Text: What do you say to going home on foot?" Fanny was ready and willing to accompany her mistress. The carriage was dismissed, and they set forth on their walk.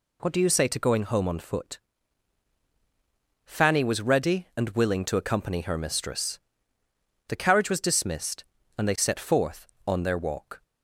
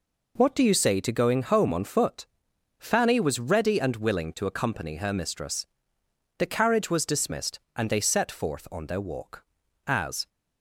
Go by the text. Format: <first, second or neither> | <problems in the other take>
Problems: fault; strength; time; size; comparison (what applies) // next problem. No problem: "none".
first | goes on to say "As"; slight; from 9.8 s on; 0.40 s long